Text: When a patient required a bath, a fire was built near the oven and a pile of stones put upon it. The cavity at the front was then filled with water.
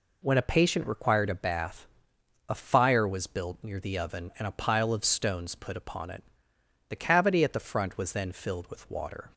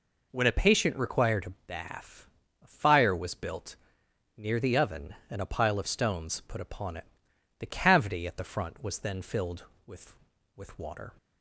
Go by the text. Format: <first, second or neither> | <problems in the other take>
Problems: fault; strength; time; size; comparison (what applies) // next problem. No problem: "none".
first | pauses between "built" and "near"; noticeable; at 3.7 s; 0.62 s long // says "with" twice; at 10.5 s